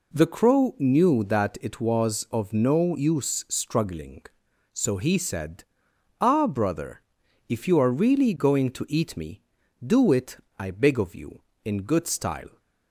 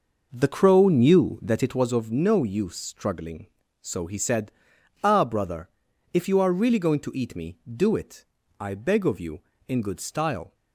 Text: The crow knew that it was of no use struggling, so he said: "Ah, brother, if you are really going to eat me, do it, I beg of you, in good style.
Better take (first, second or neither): first